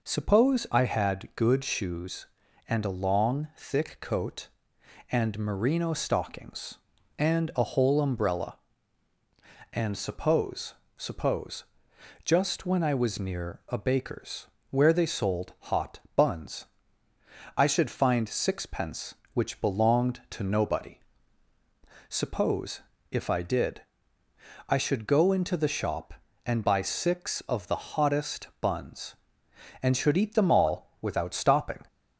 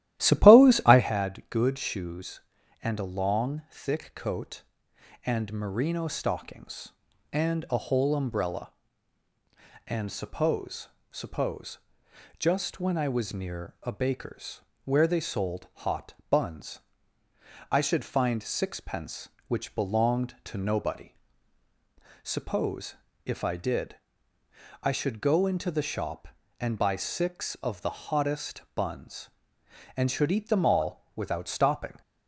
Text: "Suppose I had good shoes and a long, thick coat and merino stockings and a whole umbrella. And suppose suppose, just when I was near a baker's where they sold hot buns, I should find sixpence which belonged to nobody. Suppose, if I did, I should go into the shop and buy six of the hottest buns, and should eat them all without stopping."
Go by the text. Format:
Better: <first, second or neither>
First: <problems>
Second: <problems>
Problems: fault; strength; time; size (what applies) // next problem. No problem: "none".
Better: first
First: pauses between "suppose" and "suppose"; slight; at 10.7 s; 0.22 s long // pauses between "baker's" and "where"; slight; at 14.4 s; 0.24 s long // pauses between "hot" and "buns"; slight; at 15.9 s; 0.16 s long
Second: starts louder than the rest; strong; until 1.1 s; 13.5 dB // pauses between "suppose" and "suppose"; slight; at 10.8 s; 0.22 s long // pauses between "baker's" and "where"; slight; at 14.6 s; 0.24 s long // pauses between "hot" and "buns"; slight; at 16.1 s; 0.16 s long